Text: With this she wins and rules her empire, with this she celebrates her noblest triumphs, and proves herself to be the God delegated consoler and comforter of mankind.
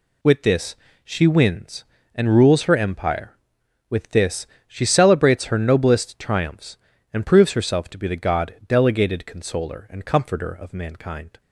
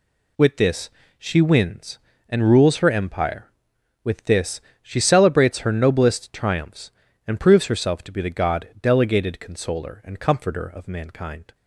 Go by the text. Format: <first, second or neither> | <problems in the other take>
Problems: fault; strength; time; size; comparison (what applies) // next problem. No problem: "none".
neither | pauses between "this" and "she"; slight; the same in both // pauses between "this" and "she"; slight; the same in both